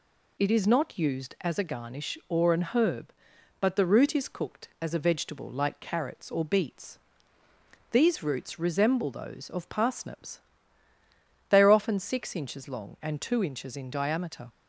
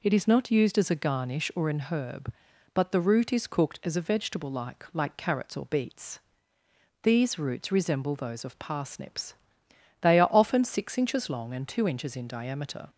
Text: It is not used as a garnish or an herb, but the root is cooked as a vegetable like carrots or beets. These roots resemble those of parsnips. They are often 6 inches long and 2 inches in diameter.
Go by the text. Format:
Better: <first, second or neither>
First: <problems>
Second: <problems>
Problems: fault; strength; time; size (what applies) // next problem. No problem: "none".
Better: first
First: none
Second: says "like" twice; at 4.9 s